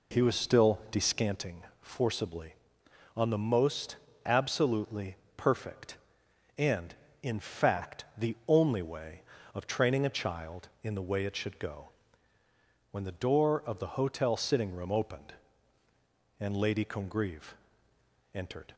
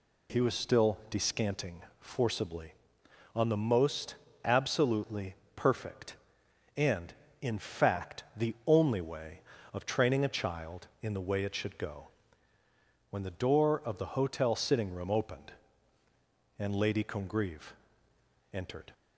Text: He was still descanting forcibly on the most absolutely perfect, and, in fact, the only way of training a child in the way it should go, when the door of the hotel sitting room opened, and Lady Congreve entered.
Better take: second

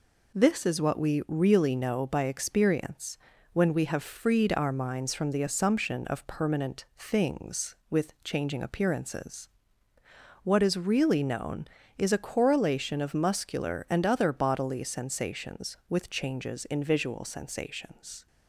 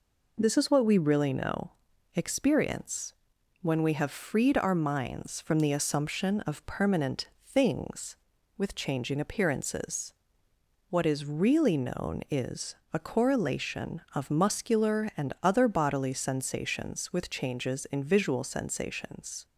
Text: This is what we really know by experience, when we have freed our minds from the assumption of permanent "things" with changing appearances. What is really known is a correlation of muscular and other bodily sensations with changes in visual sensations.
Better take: first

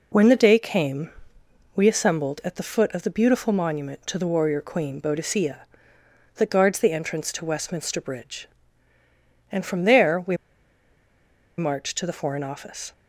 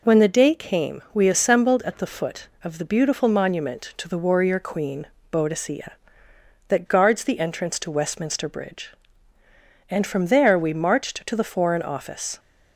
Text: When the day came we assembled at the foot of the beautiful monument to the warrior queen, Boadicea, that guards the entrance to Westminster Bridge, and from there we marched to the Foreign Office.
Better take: second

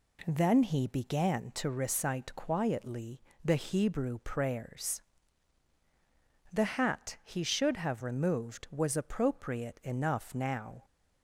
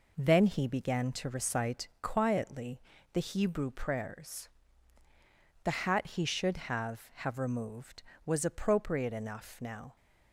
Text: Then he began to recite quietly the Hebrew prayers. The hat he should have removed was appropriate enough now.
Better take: first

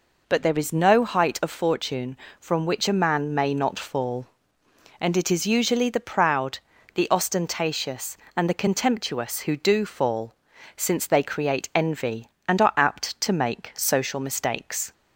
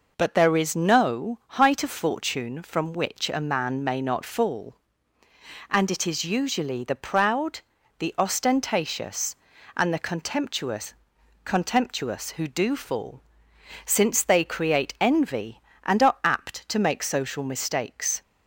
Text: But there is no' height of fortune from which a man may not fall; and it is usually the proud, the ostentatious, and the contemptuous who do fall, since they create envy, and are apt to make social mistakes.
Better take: first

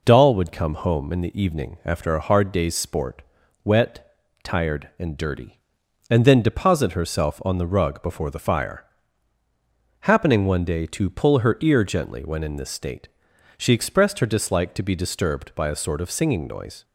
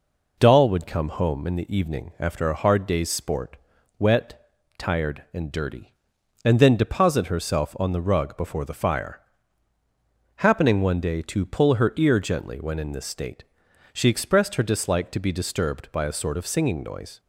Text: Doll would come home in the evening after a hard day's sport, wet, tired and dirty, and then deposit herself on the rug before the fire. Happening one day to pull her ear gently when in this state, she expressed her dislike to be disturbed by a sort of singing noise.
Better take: neither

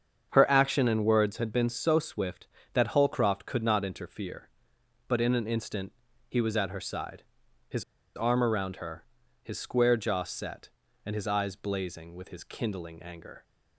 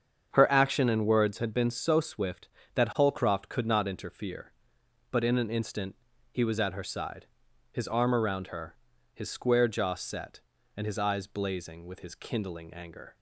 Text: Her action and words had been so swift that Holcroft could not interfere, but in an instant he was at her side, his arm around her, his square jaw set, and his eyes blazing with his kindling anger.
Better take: second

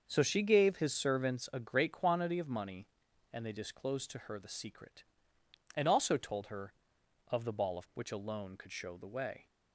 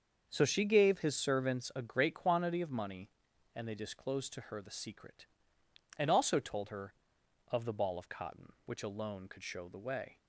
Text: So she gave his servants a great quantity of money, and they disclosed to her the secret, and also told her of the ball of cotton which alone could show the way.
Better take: second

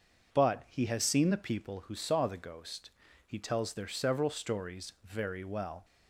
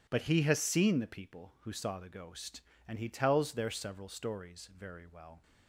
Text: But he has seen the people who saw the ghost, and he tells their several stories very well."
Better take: second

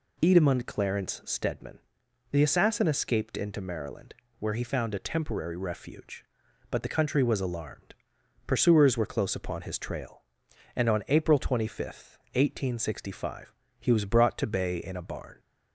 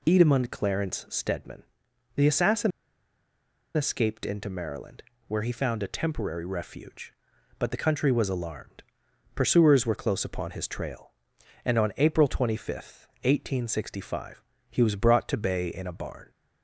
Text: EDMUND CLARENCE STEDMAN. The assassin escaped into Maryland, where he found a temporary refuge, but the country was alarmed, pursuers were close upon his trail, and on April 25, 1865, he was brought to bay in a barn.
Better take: first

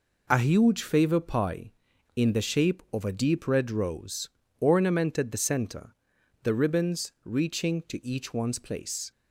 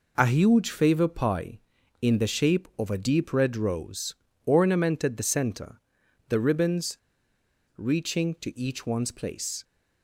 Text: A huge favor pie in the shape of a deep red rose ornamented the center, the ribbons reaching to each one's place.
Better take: first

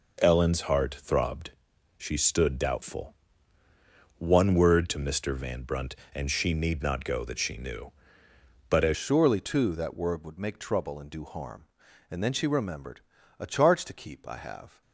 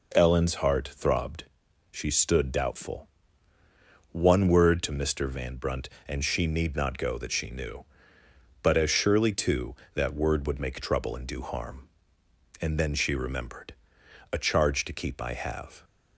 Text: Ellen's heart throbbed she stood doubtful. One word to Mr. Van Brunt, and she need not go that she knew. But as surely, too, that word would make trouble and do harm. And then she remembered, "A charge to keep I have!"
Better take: second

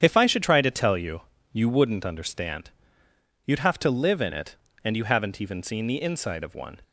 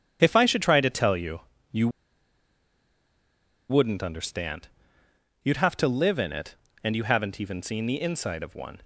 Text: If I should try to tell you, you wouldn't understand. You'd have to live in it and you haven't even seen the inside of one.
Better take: first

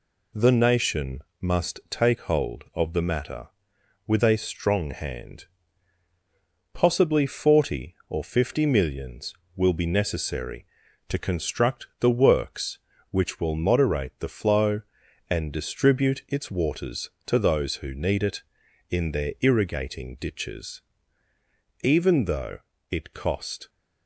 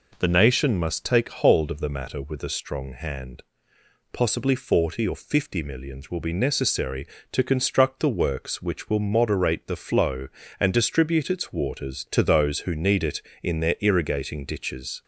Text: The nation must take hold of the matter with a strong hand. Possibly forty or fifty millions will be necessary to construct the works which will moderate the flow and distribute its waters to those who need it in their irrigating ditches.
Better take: second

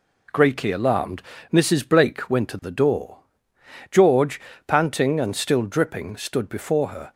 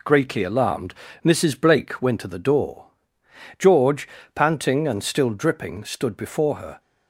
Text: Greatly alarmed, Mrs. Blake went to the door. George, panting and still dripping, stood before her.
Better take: neither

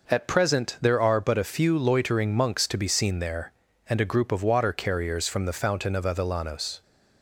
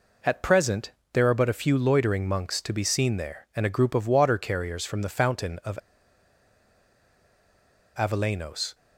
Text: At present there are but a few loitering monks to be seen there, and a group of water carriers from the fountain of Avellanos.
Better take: first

